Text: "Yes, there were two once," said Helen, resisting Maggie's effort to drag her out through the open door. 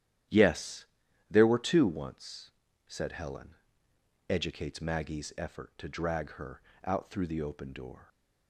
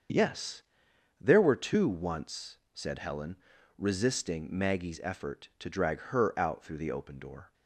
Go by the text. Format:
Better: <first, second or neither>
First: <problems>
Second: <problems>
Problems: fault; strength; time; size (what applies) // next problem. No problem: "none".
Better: second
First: starts louder than the rest; strong; until 1.7 s; 11 dB // says "educates" for "resisting"; at 4.2 s // pauses between "her" and "out"; slight; at 6.6 s; 0.24 s long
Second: starts louder than the rest; until 1.7 s; 6.5 dB